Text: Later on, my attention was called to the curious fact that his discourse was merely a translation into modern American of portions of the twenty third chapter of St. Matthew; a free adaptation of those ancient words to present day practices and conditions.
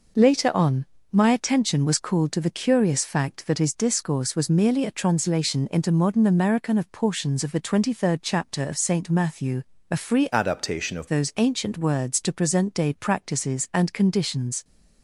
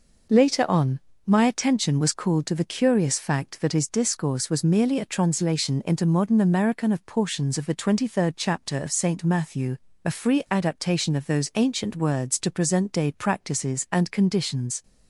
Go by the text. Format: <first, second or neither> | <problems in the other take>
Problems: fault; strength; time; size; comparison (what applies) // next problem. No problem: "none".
second | changes voice from "adaptation" to "of"; from 10.3 to 11.0 s; 0.7 s long